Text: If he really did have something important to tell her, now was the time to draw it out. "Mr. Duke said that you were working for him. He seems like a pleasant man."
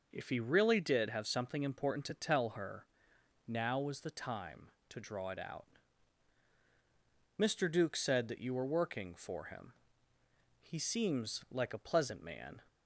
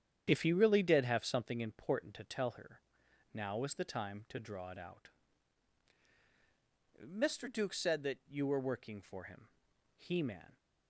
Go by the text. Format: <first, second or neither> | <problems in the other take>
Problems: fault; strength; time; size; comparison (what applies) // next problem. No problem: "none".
first | starts louder than the rest; strong; until 1.2 s; 9 dB // skips "seems like a pleasant"; at 10.2 s